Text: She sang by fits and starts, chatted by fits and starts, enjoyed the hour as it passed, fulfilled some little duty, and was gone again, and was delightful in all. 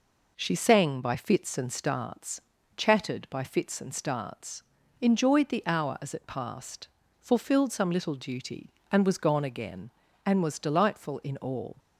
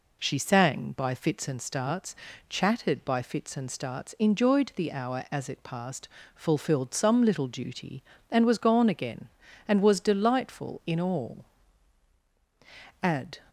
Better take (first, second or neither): first